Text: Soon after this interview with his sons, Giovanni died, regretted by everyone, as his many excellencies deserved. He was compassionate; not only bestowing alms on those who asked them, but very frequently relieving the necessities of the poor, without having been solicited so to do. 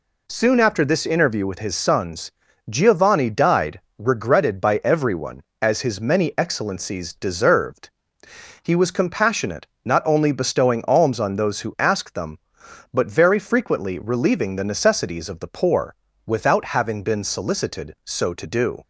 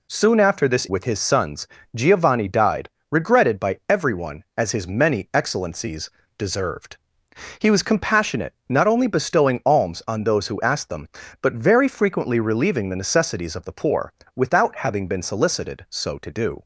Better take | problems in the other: first | skips "interview"; at 0.8 s // pauses between "excellencies" and "deserved"; slight; at 6.0 s; 0.30 s long

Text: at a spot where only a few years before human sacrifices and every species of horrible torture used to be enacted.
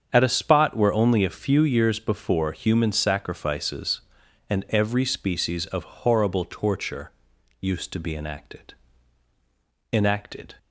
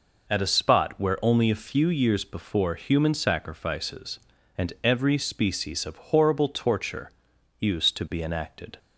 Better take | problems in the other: second | starts louder than the rest; strong; until 1.1 s; 7.5 dB // pauses between "torture" and "used"; noticeable; at 7.1 s; 0.50 s long; noticeable in the second // says "enacted" twice; at 9.9 s

